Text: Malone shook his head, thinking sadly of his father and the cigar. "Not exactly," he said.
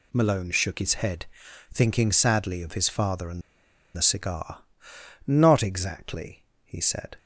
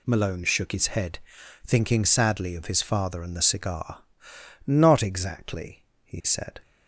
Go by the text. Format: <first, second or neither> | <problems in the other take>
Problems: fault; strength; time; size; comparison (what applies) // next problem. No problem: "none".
second | pauses between "and" and "the"; noticeable; at 3.4 s; 0.54 s long